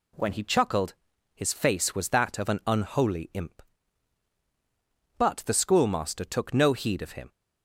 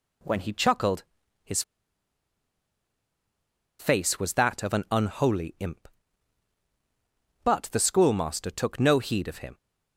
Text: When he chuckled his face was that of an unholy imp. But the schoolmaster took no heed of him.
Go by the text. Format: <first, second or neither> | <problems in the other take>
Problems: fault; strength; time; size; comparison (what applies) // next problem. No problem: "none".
first | pauses between "chuckled" and "his"; at 1.0 s; 0.40 s long; also in the first // pauses between "his" and "face"; strong; at 1.6 s; 2.1 s long